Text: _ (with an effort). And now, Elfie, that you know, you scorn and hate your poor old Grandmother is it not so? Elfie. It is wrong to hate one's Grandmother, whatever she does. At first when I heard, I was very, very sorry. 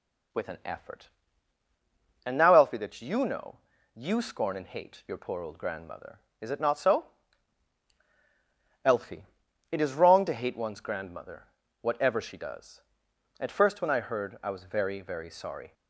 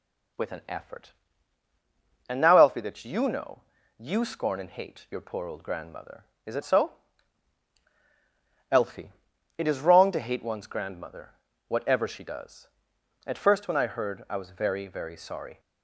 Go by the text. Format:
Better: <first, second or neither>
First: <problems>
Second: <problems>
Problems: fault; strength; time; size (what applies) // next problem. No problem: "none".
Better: first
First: none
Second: skips "not"; at 6.6 s